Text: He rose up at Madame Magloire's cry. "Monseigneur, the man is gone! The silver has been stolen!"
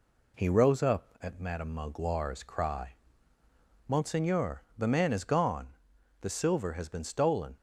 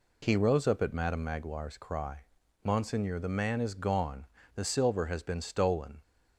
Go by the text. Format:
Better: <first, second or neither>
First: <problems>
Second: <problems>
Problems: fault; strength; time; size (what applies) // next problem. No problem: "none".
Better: neither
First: none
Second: none